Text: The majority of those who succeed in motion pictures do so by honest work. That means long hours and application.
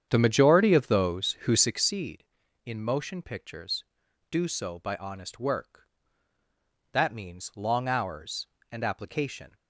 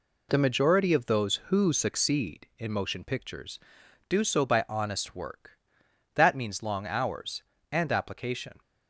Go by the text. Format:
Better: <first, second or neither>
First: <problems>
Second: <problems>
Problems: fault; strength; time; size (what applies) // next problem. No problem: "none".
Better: second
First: starts louder than the rest; strong; until 1.9 s; 8.5 dB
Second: none